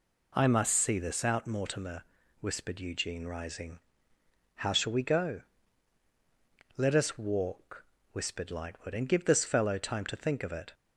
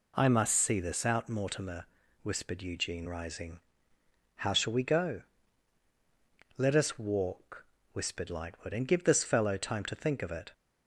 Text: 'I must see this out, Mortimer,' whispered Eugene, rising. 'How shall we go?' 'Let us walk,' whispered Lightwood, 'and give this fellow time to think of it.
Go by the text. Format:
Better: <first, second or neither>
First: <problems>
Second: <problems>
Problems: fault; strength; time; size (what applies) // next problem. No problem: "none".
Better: neither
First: none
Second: none